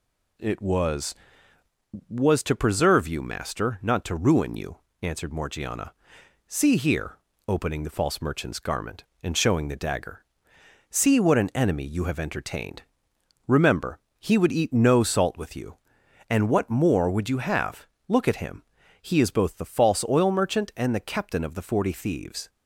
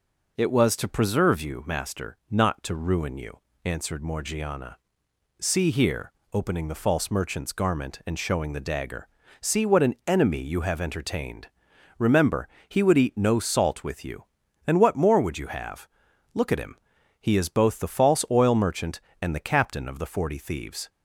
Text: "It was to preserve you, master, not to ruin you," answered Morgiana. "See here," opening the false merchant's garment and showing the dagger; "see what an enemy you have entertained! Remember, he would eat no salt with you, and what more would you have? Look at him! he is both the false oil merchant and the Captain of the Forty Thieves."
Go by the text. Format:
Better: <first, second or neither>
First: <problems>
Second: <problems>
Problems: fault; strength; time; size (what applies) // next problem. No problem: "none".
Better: second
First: says "was" twice; at 2.1 s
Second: none